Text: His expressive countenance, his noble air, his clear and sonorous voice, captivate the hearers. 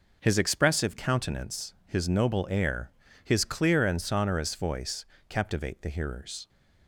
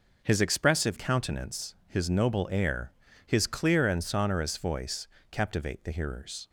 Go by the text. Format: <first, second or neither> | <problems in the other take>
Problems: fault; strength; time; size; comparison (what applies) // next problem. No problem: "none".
neither | none